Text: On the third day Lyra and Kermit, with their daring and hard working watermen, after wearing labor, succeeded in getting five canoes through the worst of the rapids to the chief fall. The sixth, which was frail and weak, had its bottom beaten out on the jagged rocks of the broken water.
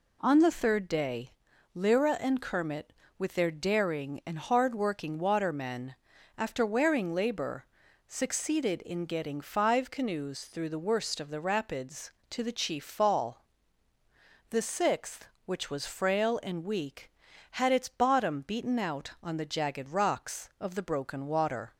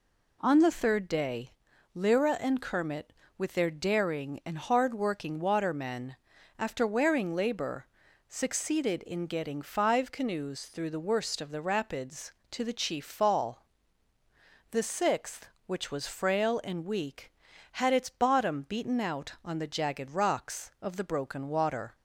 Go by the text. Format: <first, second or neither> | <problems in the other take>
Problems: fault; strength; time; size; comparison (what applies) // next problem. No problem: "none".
neither | pauses between "day" and "Lyra"; the same in both